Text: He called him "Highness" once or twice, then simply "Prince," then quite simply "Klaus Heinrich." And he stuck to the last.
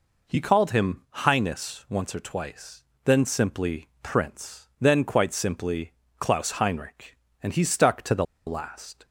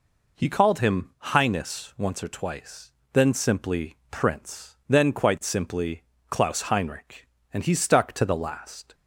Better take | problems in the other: second | pauses between "simply" and "Klaus"; slight; at 5.9 s; 0.26 s long; slight in the second // pauses between "the" and "last"; slight; at 8.2 s; 0.21 s long

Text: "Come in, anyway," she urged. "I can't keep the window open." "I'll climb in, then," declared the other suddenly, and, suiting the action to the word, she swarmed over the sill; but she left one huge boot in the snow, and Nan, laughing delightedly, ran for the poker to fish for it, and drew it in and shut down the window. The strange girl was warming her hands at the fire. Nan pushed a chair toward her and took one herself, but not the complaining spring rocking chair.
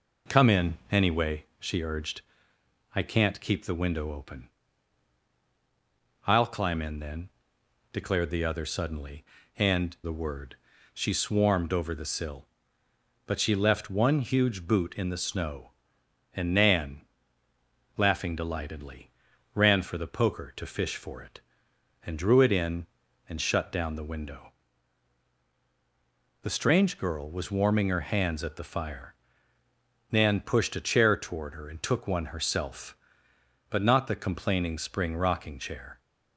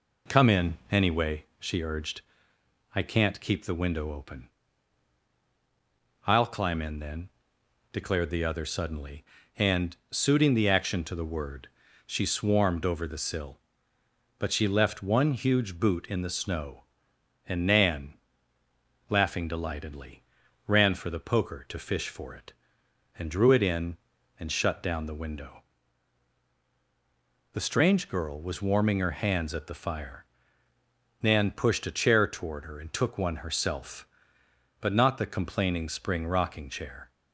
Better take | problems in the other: second | skips "suiting the action to"; at 9.9 s

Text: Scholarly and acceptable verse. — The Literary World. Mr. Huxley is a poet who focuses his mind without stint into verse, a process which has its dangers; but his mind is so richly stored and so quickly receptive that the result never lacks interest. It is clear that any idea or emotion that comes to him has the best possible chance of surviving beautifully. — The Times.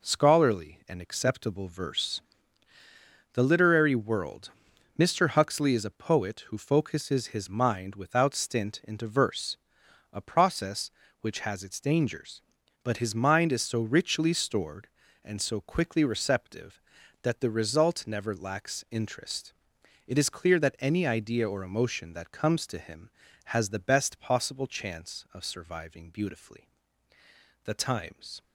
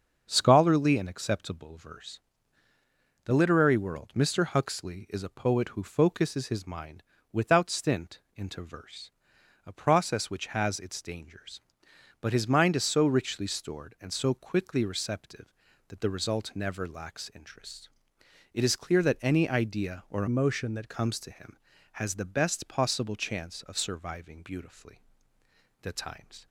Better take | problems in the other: first | starts louder than the rest; until 1.2 s; 6.5 dB // pauses between "mind" and "without"; slight; at 7.0 s; 0.30 s long // pauses between "stint" and "into"; slight; at 8.1 s; 0.16 s long // changes voice from "emotion" to "that"; from 20.2 to 20.8 s; 0.6 s long

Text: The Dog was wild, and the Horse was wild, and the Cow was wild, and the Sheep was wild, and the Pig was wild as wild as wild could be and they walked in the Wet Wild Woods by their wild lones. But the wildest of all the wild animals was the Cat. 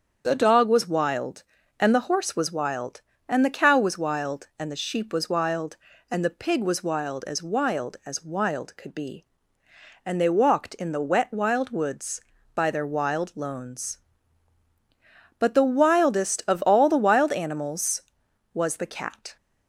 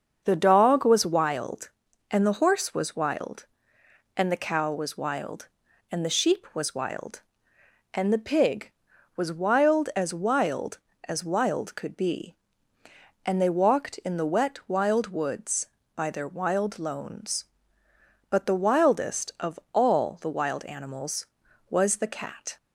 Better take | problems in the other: neither | starts louder than the rest; the same in both

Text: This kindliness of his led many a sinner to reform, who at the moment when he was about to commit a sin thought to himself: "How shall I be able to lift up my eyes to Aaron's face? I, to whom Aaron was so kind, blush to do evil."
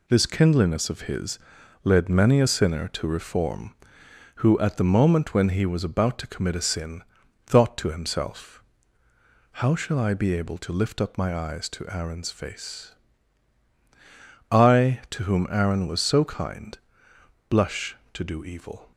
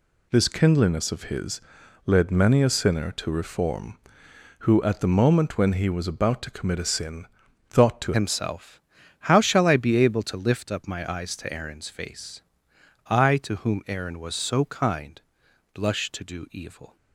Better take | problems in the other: first | pauses between "his" and "led"; at 1.6 s; 0.44 s long; also in the first // pauses between "sin" and "thought"; at 7.2 s; 0.44 s long; also in the first // changes voice at "himself"; from 8.1 s on; 8.8 s long

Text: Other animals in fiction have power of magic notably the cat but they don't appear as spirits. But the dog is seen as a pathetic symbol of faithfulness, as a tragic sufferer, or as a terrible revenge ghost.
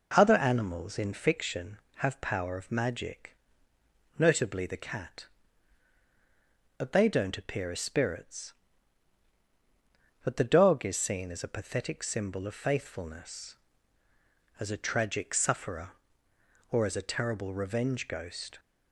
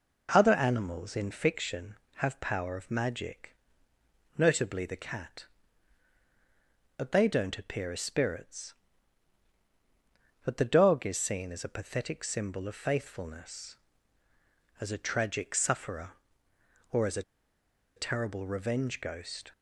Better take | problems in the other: first | pauses between "magic" and "notably"; noticeable; at 3.5 s; 0.82 s long; noticeable in the first // pauses between "a" and "terrible"; noticeable; at 17.2 s; 0.74 s long

